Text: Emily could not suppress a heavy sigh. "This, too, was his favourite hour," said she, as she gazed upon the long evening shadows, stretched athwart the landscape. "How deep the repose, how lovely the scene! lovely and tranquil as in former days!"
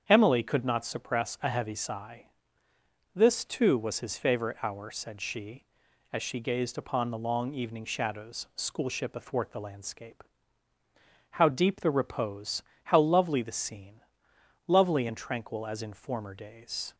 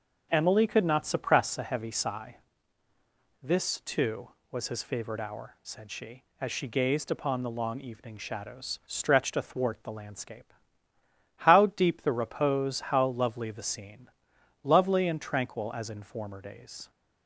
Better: second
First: starts louder than the rest; strong; until 1.0 s; 7.5 dB // says "schoolship" for "stretched"; at 8.5 s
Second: none

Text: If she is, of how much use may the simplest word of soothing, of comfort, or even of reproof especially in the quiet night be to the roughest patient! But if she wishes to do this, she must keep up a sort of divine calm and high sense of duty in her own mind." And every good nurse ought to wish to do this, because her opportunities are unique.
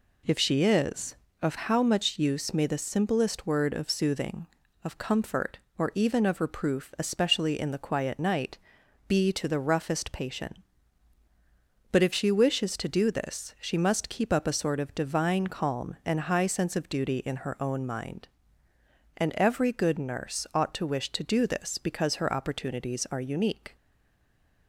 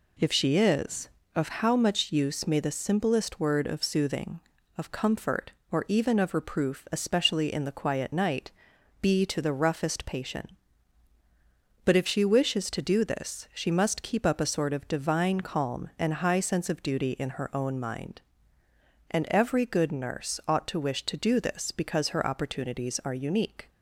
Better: second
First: pauses between "night" and "be"; noticeable; at 8.5 s; 0.50 s long // stays silent after the last word; slight; from 23.7 s on; 0.9 s long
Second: pauses between "night" and "be"; noticeable; at 8.4 s; 0.50 s long

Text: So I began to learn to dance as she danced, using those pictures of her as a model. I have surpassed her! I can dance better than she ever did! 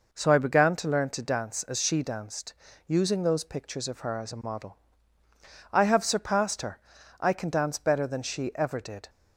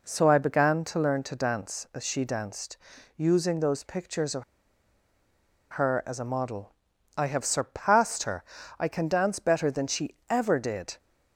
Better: first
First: none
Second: pauses between "of" and "her"; strong; at 4.4 s; 1.2 s long

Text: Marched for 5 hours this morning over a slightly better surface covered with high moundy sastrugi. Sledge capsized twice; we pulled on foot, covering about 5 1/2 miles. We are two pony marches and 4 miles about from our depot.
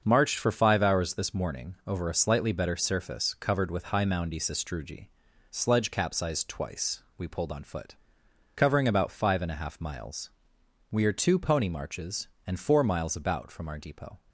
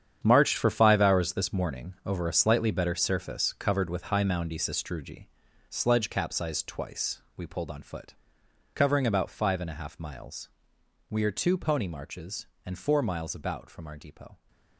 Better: first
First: starts louder than the rest; until 1.0 s; 6.5 dB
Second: gets quieter; strong; throughout; 12 dB // starts louder than the rest; strong; until 1.2 s; 8.5 dB

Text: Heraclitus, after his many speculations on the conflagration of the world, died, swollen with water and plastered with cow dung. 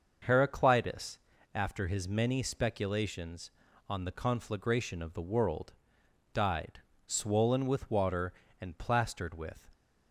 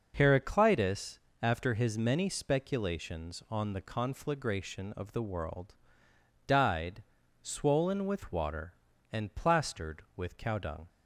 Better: second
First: starts louder than the rest; noticeable; until 1.5 s; 6 dB // stops before "cow dung"; at 9.7 s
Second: none

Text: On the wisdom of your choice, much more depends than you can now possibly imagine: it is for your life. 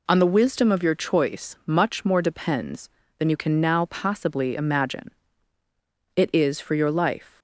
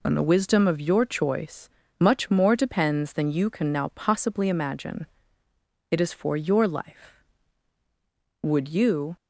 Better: first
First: none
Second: goes on to say "Would you"; noticeable; from 8.4 s on; 0.74 s long

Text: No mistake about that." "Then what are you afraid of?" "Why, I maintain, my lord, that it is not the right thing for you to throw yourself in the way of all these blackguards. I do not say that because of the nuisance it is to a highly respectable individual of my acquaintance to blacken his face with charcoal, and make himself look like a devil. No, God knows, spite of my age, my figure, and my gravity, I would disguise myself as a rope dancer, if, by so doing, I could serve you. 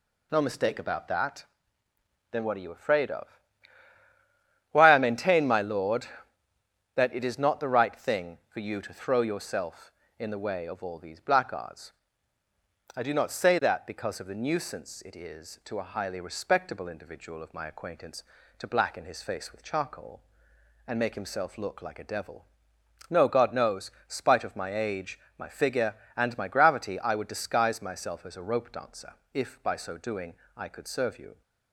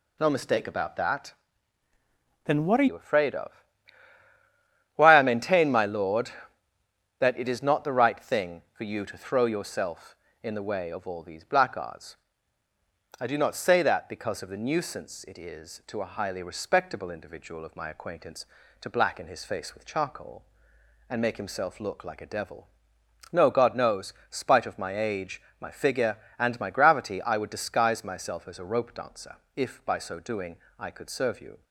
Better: first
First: none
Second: changes voice from "Then" to "are"; from 2.4 to 2.8 s; 0.4 s long

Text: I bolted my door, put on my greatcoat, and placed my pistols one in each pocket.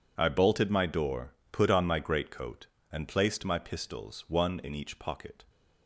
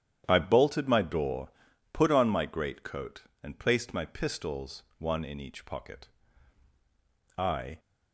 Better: first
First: none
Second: starts louder than the rest; strong; until 1.2 s; 10 dB // pauses between "pistols" and "one"; slight; at 4.8 s; 0.16 s long // goes on to say "I"; slight; from 7.3 s on; 0.42 s long

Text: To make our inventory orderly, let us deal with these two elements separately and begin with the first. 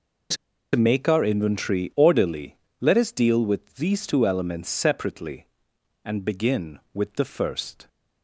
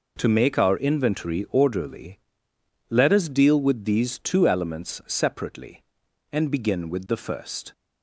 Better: second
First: pauses between "To" and "make"; at 0.3 s; 0.39 s long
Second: none

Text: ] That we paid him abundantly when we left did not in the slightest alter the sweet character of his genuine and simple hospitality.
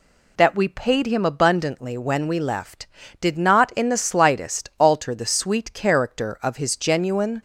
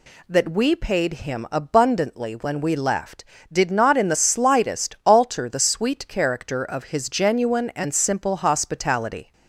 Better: second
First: stops before "and simple hospitality"; at 7.3 s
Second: none

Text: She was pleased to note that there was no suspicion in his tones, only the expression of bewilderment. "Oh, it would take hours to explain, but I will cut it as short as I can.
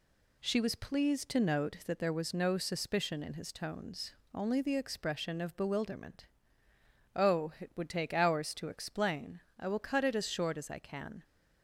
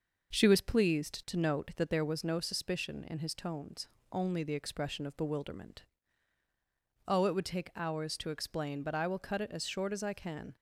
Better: second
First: skips "but"; at 9.4 s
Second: none

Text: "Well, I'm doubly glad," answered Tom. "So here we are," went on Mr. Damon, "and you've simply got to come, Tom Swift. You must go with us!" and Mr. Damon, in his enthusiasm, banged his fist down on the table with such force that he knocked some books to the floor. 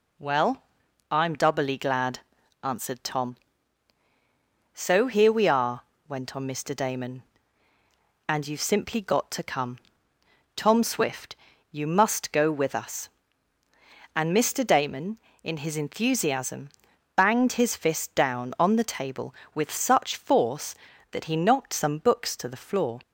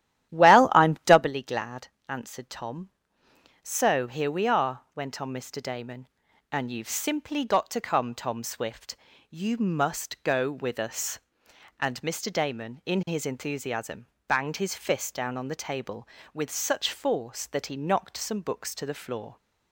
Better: first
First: none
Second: starts louder than the rest; strong; until 1.3 s; 12.5 dB

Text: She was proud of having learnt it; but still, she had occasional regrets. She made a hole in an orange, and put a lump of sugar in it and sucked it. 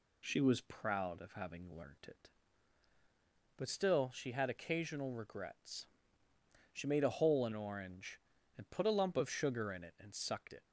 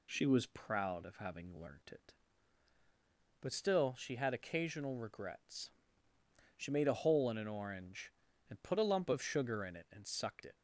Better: second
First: skips "an"; at 7.5 s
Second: none

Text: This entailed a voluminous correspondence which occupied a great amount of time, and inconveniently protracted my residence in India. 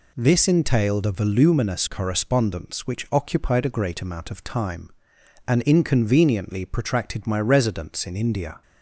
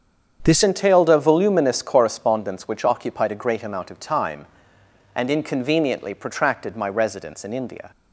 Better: first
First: none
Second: starts louder than the rest; strong; until 1.4 s; 7.5 dB // changes voice at "entailed"; from 0.6 s on; 7.3 s long

